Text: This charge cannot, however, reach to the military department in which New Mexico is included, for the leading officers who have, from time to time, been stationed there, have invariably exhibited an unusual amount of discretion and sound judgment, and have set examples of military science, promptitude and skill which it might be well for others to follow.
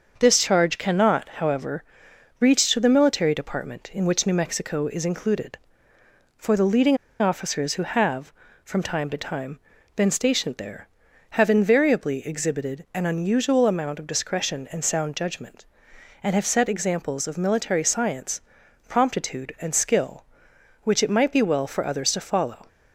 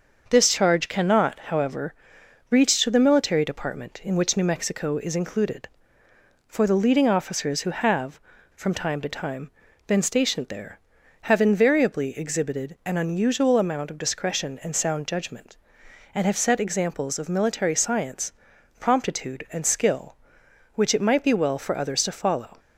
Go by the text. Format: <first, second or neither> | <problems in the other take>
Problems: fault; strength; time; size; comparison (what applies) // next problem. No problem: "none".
second | starts louder than the rest; until 1.1 s; 6.5 dB; also in the second // pauses between "leading" and "officers"; slight; at 6.9 s; 0.23 s long